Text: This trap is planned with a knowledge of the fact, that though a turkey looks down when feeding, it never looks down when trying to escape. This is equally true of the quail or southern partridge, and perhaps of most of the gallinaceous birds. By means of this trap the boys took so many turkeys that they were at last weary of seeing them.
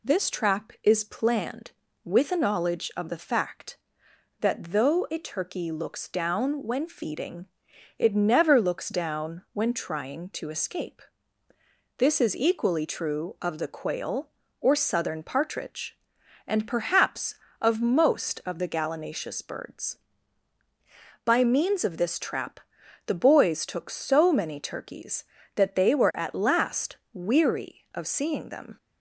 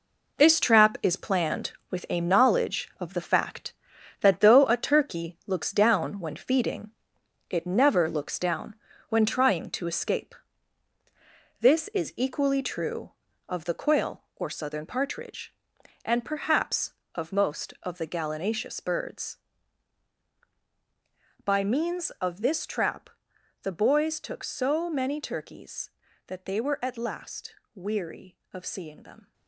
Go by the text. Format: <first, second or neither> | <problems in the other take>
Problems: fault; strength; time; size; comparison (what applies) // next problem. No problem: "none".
first | gets quieter; strong; throughout; 9 dB // pauses between "down" and "when"; slight; at 8.7 s; 0.34 s long // pauses between "trap" and "the"; noticeable; at 23.0 s; 0.54 s long; noticeable in the first // pauses between "last" and "weary"; slight; at 27.5 s; 0.20 s long; slight in the first